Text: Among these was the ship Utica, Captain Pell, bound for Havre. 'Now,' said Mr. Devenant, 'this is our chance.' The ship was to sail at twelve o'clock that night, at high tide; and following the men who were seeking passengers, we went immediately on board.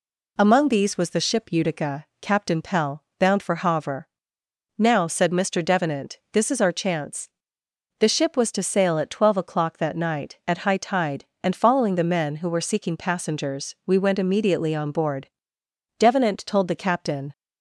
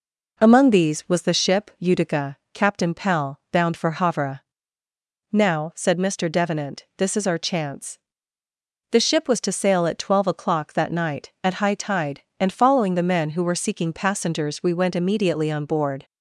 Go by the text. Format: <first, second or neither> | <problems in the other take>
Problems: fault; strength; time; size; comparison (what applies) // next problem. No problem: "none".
second | goes on to say "Devenant told the captain"; from 15.9 s on; 1.3 s long